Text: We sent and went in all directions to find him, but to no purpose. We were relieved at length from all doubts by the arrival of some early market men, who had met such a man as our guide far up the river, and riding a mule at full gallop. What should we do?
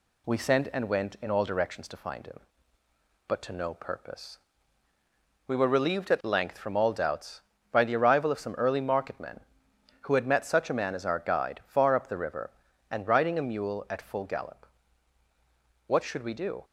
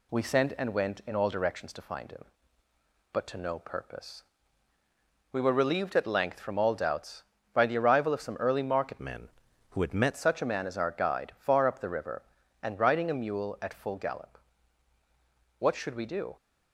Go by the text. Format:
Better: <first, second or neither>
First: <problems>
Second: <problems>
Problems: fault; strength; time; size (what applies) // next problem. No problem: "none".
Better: first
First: none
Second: changes voice from "men" to "met"; from 8.9 to 10.1 s; 1.2 s long